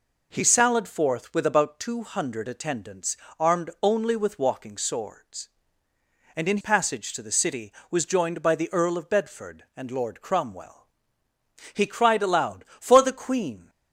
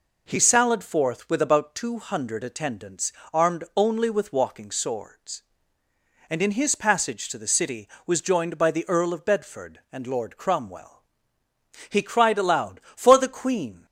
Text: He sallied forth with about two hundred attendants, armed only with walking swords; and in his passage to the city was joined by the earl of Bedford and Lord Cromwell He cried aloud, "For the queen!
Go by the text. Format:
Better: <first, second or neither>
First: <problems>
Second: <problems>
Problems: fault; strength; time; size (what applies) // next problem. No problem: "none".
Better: second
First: skips "his"; at 6.6 s // pauses between "Cromwell" and "He"; noticeable; at 10.8 s; 0.86 s long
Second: pauses between "Cromwell" and "He"; noticeable; at 11.0 s; 0.86 s long